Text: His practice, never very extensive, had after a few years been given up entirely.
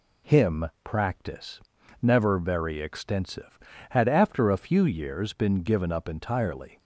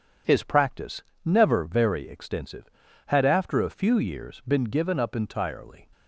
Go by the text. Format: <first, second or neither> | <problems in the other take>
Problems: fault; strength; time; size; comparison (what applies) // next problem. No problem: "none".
second | says "Him" for "His"; at 0.2 s